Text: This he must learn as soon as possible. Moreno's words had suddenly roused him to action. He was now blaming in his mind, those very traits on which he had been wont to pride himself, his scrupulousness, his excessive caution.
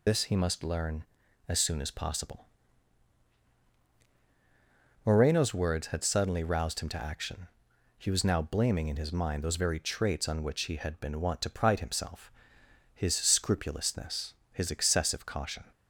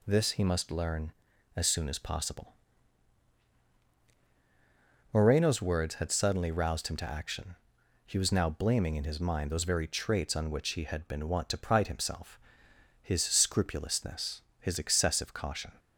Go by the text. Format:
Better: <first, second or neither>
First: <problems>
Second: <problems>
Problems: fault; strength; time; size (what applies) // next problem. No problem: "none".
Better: second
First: loses the start of "This"; at 0.0 s; 125 ms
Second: none